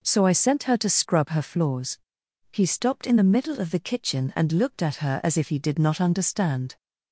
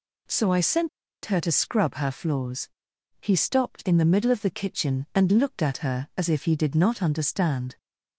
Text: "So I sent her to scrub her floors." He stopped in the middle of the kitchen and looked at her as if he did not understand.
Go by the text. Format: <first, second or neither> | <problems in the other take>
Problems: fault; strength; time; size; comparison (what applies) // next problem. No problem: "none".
first | pauses between "sent" and "her"; slight; at 0.8 s; 0.36 s long